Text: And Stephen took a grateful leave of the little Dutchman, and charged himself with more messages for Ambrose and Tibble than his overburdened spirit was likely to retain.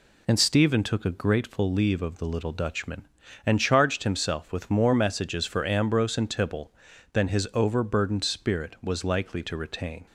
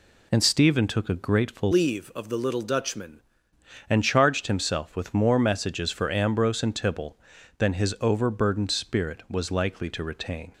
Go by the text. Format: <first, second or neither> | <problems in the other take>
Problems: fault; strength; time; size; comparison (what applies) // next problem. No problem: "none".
first | changes voice from "leave" to "Dutchman"; from 1.7 to 3.2 s; 1.5 s long